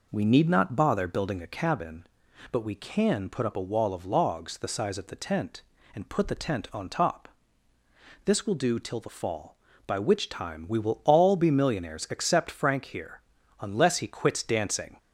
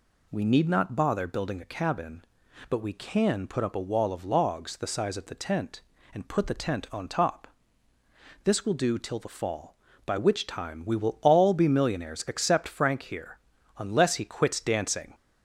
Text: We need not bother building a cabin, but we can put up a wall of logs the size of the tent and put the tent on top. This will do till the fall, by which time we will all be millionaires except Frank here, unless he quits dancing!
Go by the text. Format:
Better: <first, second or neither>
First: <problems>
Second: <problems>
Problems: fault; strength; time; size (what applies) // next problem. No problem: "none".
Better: second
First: starts louder than the rest; noticeable; until 1.8 s; 4.5 dB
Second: none